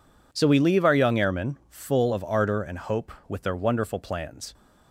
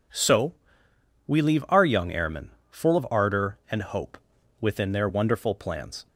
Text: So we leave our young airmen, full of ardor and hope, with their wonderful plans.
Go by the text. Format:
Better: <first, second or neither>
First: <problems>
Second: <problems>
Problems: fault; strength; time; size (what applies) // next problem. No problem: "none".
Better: first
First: none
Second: pauses between "So" and "we"; noticeable; at 0.5 s; 0.72 s long // says "within" for "with"; at 4.6 s